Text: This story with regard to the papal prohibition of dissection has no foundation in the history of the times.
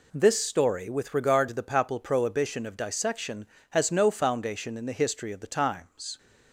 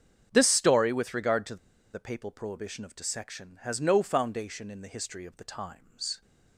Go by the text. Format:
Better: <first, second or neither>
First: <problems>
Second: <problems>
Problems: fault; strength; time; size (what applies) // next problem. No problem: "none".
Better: first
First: none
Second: starts louder than the rest; strong; until 1.3 s; 7.5 dB // pauses between "to" and "the"; at 1.5 s; 0.38 s long